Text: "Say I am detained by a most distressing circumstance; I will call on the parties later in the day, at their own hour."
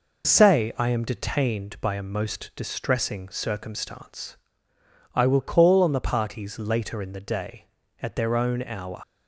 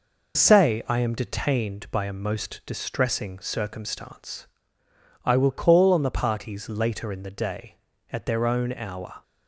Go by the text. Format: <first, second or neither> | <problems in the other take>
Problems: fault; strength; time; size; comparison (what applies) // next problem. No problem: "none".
second | leaves "hour" unfinished; at 9.0 s; 85 ms